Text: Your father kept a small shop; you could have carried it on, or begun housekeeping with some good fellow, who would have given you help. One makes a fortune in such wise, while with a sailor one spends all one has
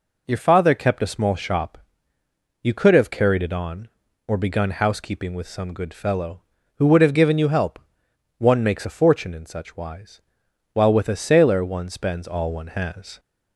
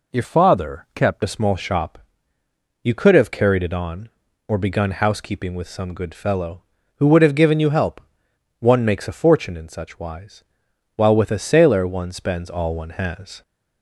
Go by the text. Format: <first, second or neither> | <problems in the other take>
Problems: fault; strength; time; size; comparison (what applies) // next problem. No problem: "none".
first | changes voice from "father" to "kept"; from 0.2 to 1.2 s; 1.0 s long